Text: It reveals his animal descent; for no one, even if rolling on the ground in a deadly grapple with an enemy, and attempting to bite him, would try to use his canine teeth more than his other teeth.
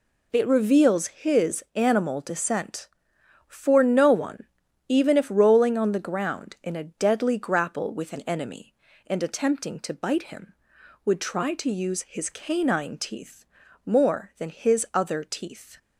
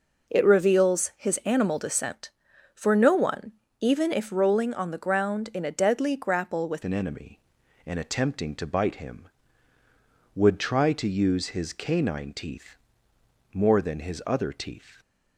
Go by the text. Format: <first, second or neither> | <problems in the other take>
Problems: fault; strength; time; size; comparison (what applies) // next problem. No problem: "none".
first | changes voice at "an"; from 6.8 s on; 8.2 s long // pauses between "teeth" and "more"; noticeable; at 12.7 s; 0.78 s long; also in the first